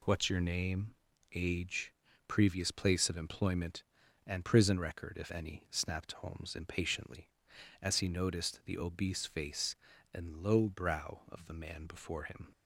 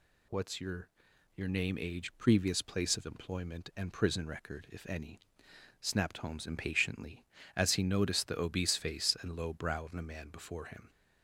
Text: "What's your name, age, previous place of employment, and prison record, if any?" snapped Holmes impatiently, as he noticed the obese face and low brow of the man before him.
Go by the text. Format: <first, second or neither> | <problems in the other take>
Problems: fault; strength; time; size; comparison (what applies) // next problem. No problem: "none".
first | says "your" twice; at 1.3 s